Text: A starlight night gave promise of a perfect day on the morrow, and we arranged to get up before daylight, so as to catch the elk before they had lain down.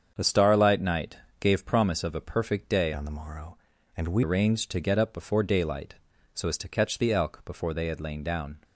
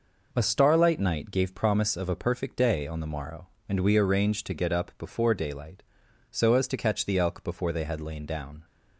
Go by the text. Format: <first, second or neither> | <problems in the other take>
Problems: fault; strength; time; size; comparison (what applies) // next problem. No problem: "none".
second | starts louder than the rest; strong; until 1.1 s; 7.5 dB // pauses between "night" and "gave"; slight; at 1.1 s; 0.22 s long // changes voice from "on" to "we"; from 2.9 to 4.2 s; 1.3 s long